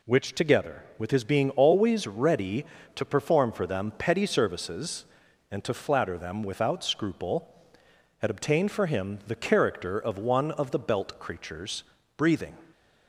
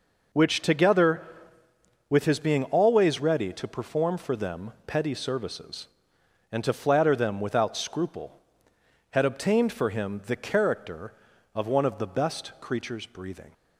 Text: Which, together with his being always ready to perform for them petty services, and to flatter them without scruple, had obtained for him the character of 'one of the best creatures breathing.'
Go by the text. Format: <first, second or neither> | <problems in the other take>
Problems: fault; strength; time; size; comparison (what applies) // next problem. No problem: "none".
second | says "belt" for "best"; at 10.7 s // pauses between "creatures" and "breathing"; slight; at 11.8 s; 0.32 s long